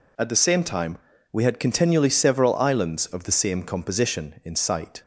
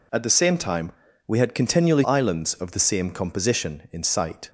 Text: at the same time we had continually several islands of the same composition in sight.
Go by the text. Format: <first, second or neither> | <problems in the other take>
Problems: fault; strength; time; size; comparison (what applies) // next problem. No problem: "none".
first | pauses between "time" and "we"; slight; at 0.9 s; 0.36 s long; slight in the first // skips "several"; at 2.0 s